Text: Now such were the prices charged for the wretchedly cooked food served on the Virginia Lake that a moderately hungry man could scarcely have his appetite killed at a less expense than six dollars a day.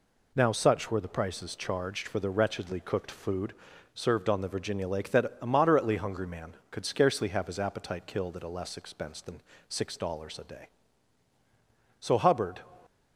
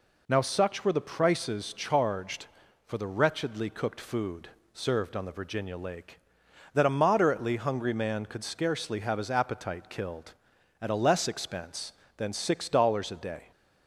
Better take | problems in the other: second | pauses between "food" and "served"; at 3.5 s; 0.42 s long; slight in the second // pauses between "than" and "six"; slight; at 9.4 s; 0.28 s long // goes on to say "So Hubbard"; noticeable; from 11.9 s on; 0.62 s long

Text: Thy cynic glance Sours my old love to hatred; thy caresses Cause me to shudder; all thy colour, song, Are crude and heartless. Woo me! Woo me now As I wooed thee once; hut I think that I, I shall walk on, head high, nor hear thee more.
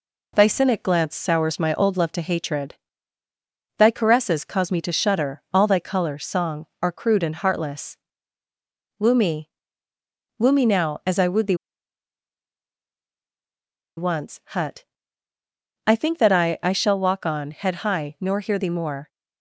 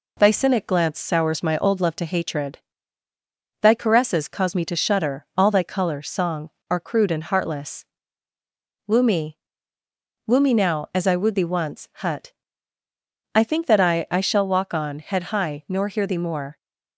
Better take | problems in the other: second | pauses between "thee" and "once"; strong; at 11.5 s; 2.4 s long // pauses between "hut" and "I"; at 14.8 s; 1.0 s long; also in the second

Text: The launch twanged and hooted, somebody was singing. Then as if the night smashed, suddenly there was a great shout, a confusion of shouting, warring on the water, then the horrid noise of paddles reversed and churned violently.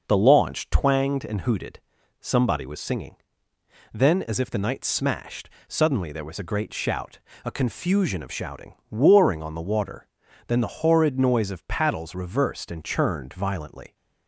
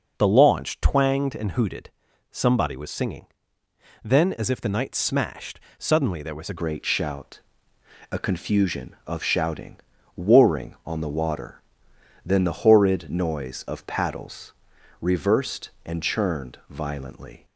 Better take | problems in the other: first | changes voice at "great"; from 6.5 s on; 10.9 s long // pauses between "paddles" and "reversed"; noticeable; at 14.5 s; 0.50 s long

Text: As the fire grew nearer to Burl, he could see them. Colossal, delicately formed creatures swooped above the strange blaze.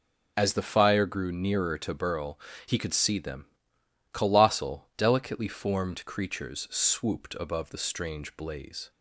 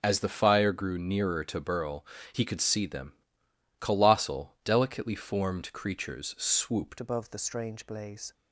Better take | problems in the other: first | changes voice at "above"; from 6.9 s on; 1.4 s long

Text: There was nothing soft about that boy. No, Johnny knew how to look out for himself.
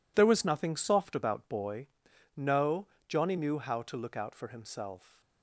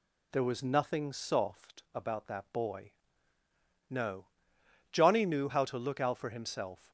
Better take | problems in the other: second | skips "that"; at 1.4 s

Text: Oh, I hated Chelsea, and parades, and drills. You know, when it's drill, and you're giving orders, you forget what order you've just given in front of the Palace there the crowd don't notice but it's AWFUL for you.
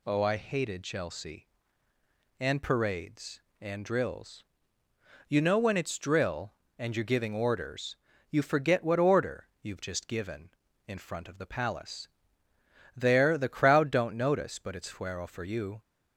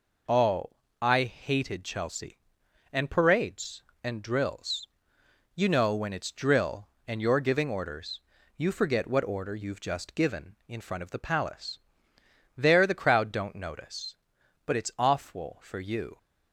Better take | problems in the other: second | pauses between "order" and "you've"; slight; at 9.4 s; 0.16 s long // pauses between "Palace" and "there"; noticeable; at 12.0 s; 0.86 s long; noticeable in the second // says "Fuero" for "AWFUL"; at 14.9 s

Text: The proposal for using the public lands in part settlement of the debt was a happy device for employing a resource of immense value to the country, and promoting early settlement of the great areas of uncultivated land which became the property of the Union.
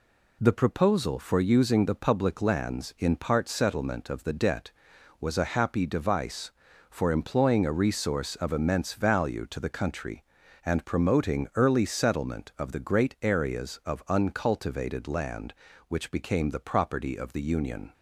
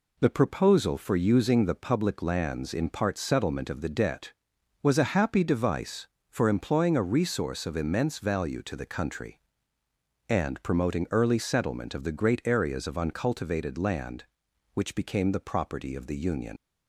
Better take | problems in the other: first | leaves "Union" unfinished; at 16.5 s; 80 ms

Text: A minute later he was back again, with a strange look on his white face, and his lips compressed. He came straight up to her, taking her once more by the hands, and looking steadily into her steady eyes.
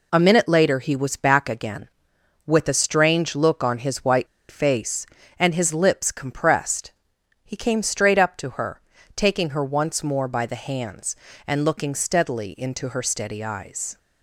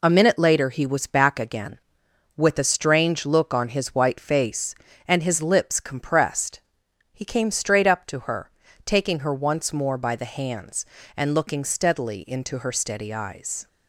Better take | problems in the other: second | pauses between "white" and "face"; slight; at 4.2 s; 0.22 s long

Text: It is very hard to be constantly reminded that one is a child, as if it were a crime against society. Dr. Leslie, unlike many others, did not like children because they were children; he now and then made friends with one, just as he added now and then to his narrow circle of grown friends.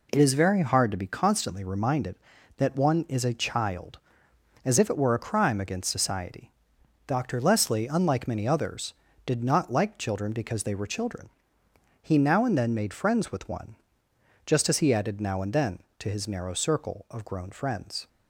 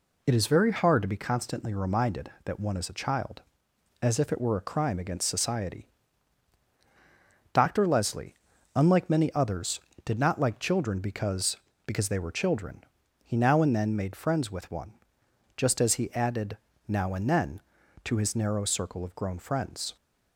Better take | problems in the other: first | says "because" twice; at 11.8 s // pauses between "added" and "now"; slight; at 16.5 s; 0.30 s long

